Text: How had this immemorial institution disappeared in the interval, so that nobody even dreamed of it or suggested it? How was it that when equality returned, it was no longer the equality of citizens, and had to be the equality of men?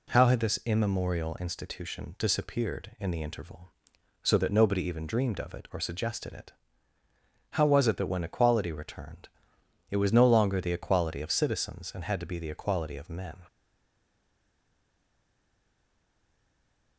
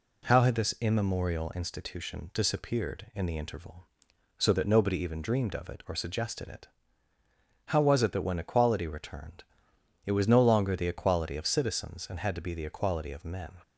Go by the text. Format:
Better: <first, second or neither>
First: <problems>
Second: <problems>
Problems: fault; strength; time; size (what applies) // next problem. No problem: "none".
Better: second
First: stays silent after the last word; strong; from 13.4 s on; 3.5 s long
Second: none